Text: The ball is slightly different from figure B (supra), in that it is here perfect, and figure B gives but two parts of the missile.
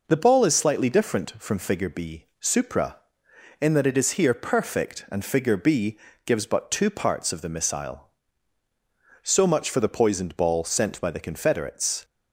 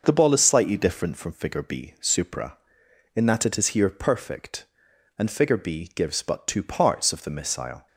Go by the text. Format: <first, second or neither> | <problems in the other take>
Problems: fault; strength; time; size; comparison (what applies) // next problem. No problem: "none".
second | pauses between "B" and "gives"; slight; at 5.9 s; 0.30 s long // goes on to say "So much for the poisoned ball sent by the Confederates"; strong; from 9.2 s on; 2.8 s long